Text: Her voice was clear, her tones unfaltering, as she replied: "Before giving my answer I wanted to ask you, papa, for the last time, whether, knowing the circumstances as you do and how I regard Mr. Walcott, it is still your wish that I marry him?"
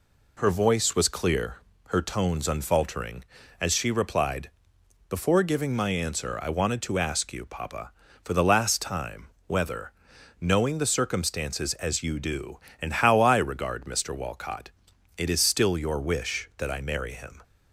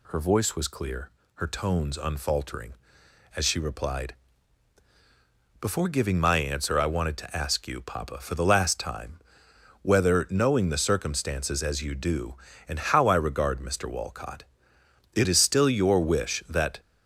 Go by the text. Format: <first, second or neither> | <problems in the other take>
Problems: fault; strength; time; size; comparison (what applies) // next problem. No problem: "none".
first | stops before "I marry him"; at 16.7 s